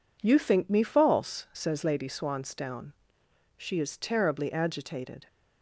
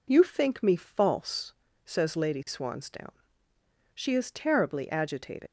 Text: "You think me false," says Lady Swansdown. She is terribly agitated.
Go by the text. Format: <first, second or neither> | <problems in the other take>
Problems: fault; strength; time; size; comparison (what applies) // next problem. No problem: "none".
first | leaves "agitated" unfinished; at 5.4 s; 75 ms